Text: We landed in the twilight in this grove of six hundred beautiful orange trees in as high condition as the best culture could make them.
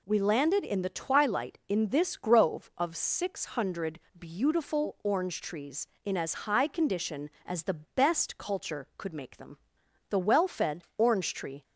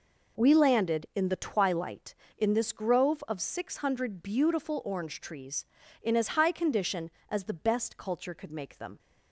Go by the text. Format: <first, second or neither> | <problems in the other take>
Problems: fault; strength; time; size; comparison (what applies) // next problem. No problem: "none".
second | pauses between "hundred" and "beautiful"; slight; at 4.0 s; 0.18 s long // goes on to say "The well fed orange tree"; from 10.0 s on; 1.5 s long